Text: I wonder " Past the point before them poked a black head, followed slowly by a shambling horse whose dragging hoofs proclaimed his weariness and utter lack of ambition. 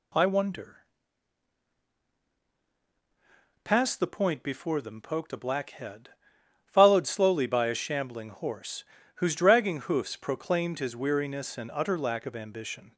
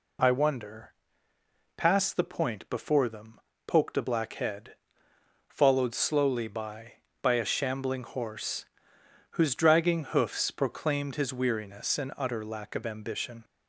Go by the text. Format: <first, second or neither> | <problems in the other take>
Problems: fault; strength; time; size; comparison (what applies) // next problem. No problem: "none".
first | pauses between "them" and "poked"; slight; at 3.4 s; 0.26 s long // says "by" twice; at 7.2 s // pauses between "horse" and "whose"; noticeable; at 8.6 s; 0.66 s long; slight in the first